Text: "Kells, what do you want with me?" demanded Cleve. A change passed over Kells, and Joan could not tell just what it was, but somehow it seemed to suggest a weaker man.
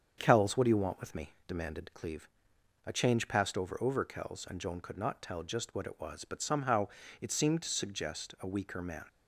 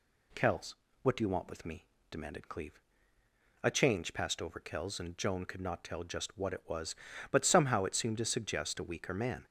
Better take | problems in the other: second | starts louder than the rest; strong; until 1.1 s; 7 dB // says "over" twice; at 3.7 s // pauses between "somehow" and "it"; slight; at 6.8 s; 0.32 s long

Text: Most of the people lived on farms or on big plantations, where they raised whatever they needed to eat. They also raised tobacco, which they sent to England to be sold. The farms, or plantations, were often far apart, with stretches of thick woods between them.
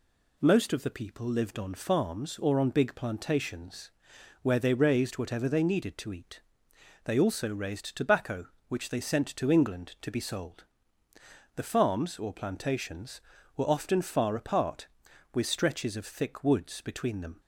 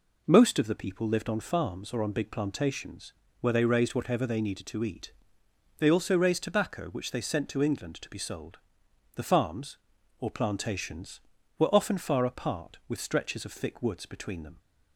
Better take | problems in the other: neither | none

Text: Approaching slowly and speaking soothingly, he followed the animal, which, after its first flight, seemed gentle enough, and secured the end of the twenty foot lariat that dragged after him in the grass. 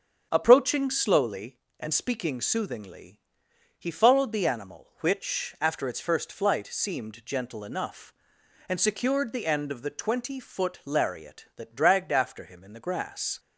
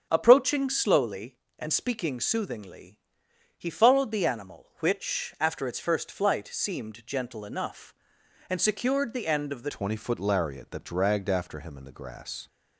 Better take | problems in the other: first | starts louder than the rest; strong; until 1.1 s; 7 dB; strong in the first // changes voice at "twenty"; from 9.6 s on; 2.8 s long

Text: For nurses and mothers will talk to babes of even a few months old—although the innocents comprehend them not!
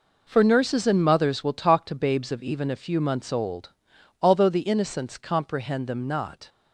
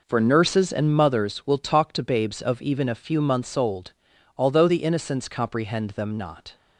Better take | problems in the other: neither | none

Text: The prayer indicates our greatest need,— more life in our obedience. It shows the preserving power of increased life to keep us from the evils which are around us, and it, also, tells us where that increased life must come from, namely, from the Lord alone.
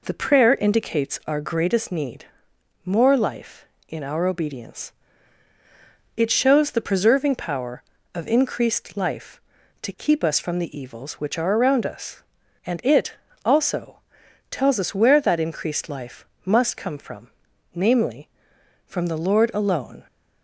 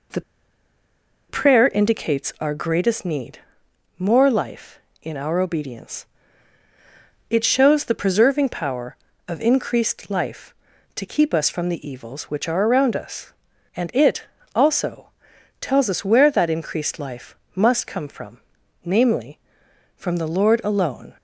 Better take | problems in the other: first | pauses between "The" and "prayer"; at 0.2 s; 1.0 s long // pauses between "life" and "must"; slight; at 17.3 s; 0.20 s long; slight in the first

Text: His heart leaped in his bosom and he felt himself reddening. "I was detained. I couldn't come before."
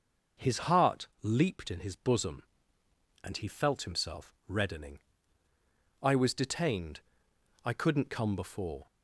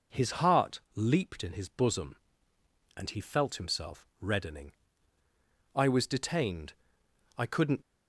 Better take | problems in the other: first | stops before "come before"; at 7.8 s

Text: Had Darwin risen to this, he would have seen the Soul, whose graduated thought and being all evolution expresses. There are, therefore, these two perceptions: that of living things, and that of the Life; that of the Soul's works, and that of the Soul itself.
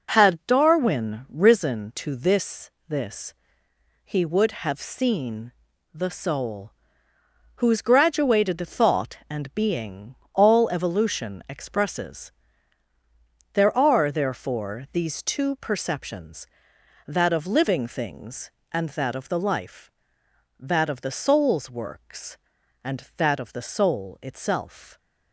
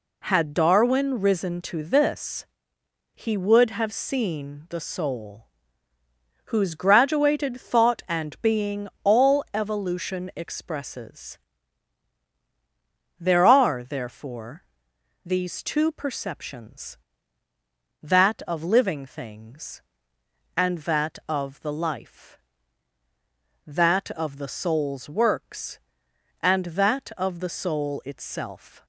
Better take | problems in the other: second | says "this" twice; at 2.8 s // pauses between "seen" and "the"; at 5.5 s; 0.42 s long // pauses between "being" and "all"; slight; at 10.1 s; 0.18 s long; slight in the second

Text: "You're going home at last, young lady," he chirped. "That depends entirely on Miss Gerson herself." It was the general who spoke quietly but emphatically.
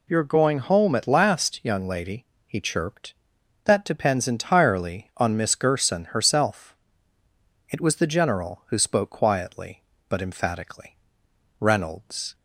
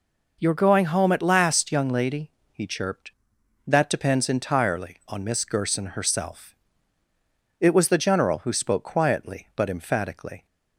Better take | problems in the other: second | goes on to say "Reynolds"; noticeable; from 11.6 s on; 0.74 s long

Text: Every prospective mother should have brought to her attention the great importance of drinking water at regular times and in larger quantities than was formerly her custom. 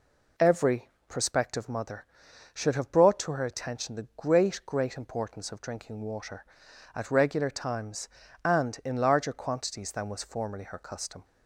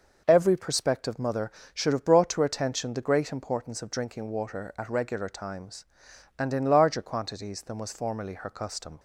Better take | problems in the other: second | pauses between "Every" and "prospective"; slight; at 0.9 s; 0.18 s long // says "great" twice; at 4.6 s

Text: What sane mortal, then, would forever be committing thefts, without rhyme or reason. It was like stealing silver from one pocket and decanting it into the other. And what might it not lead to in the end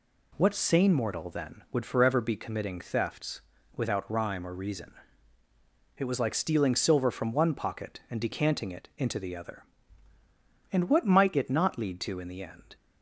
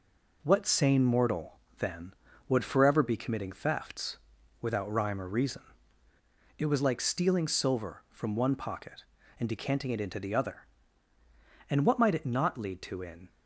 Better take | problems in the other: first | stops before "the end"; at 13.2 s

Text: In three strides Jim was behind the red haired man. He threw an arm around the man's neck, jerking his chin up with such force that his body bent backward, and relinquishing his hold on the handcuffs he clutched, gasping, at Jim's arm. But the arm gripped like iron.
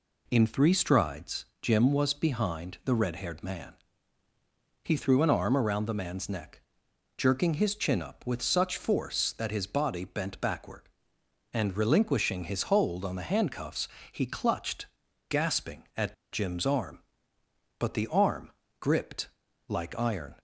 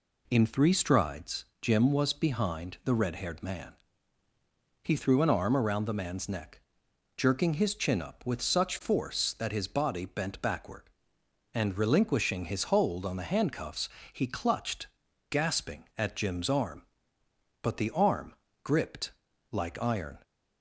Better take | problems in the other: second | pauses between "strides" and "Jim"; slight; at 1.4 s; 0.18 s long; slight in the second // pauses between "handcuffs" and "he"; slight; at 13.8 s; 0.24 s long; slight in the second // pauses between "at" and "Jim's"; slight; at 16.1 s; 0.17 s long // pauses between "arm" and "gripped"; slight; at 18.5 s; 0.30 s long; slight in the second // pauses between "gripped" and "like"; at 19.2 s; 0.42 s long; also in the second

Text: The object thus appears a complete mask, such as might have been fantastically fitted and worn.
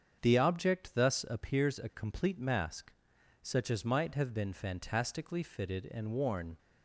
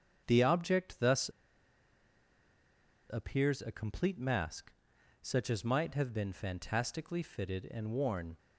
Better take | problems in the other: first | starts louder than the rest; strong; until 1.2 s; 7.5 dB; strong in the first // pauses between "thus" and "appears"; strong; at 1.2 s; 1.8 s long

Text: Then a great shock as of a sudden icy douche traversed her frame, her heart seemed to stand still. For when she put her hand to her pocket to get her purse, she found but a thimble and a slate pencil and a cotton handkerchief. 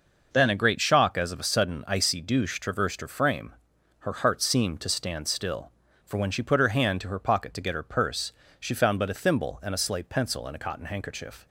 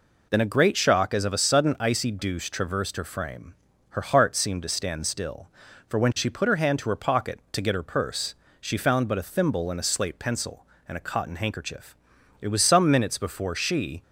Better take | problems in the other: first | goes on to say "It was some minutes before she"; from 12.3 s on; 1.6 s long

